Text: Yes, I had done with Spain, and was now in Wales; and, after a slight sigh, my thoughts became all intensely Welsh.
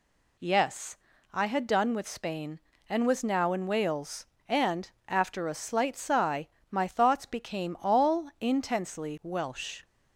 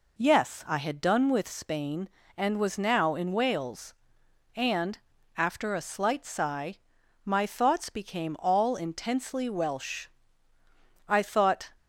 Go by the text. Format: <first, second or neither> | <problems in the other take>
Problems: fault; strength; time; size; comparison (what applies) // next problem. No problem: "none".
first | goes on to say "I thought"; noticeable; from 11.0 s on; 0.62 s long